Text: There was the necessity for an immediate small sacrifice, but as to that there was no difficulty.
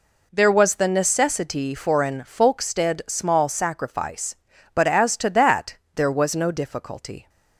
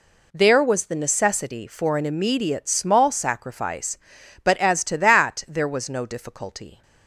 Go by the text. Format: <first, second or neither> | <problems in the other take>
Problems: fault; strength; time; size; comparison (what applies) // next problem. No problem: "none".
second | says "folkstead" for "immediate"; at 2.2 s // pauses between "that" and "there"; slight; at 5.7 s; 0.18 s long